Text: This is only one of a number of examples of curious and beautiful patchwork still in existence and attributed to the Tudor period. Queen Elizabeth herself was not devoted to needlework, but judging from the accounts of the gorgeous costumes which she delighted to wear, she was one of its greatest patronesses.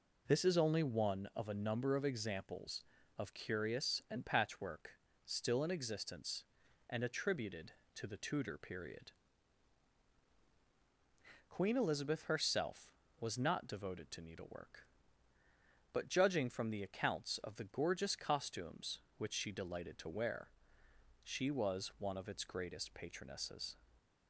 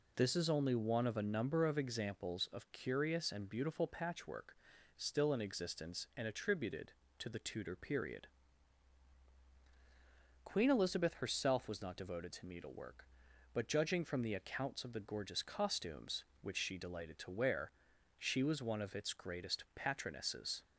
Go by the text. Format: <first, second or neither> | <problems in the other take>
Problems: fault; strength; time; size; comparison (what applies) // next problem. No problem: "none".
second | skips "beautiful"; at 4.2 s // pauses between "patchwork" and "still"; slight; at 4.9 s; 0.34 s long; also in the second